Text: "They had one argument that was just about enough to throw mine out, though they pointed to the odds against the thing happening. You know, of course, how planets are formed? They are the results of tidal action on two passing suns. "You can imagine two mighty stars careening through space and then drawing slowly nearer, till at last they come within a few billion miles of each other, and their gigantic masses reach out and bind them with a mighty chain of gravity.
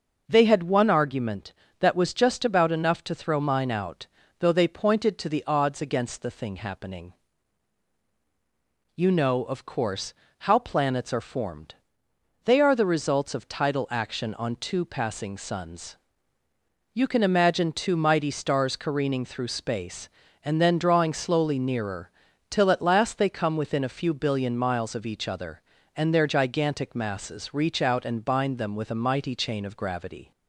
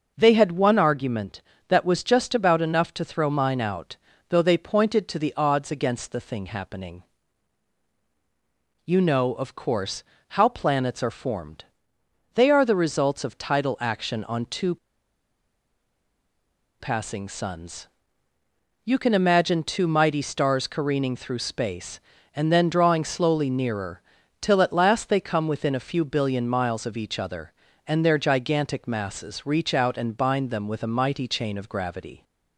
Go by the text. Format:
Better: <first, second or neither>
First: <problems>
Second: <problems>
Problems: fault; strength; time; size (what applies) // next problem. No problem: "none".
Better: first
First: none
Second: pauses between "two" and "passing"; strong; at 14.7 s; 2.0 s long